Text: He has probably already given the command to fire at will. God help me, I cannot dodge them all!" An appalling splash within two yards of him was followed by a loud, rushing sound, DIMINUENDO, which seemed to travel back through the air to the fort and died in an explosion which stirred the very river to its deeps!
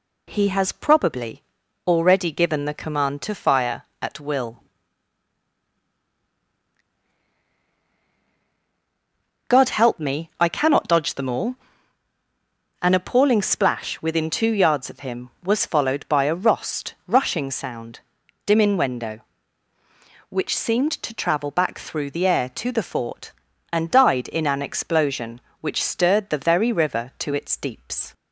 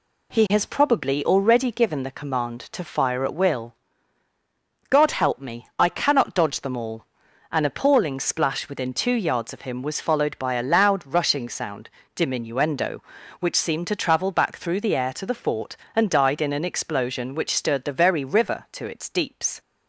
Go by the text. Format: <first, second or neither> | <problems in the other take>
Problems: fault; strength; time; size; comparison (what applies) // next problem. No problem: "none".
second | pauses between "probably" and "already"; at 1.4 s; 0.44 s long // says "rost" for "loud"; at 16.3 s